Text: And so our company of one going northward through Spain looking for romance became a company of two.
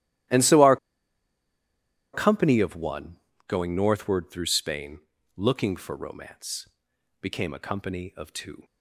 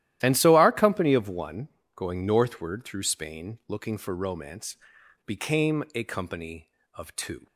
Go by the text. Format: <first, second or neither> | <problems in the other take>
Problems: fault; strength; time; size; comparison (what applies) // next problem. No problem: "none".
second | starts louder than the rest; strong; until 2.6 s; 13.5 dB; strong in the second // pauses between "our" and "company"; strong; at 0.7 s; 1.3 s long // pauses between "one" and "going"; slight; at 3.1 s; 0.30 s long; slight in the second // pauses between "Spain" and "looking"; at 4.9 s; 0.38 s long // pauses between "romance" and "became"; noticeable; at 6.6 s; 0.54 s long; noticeable in the second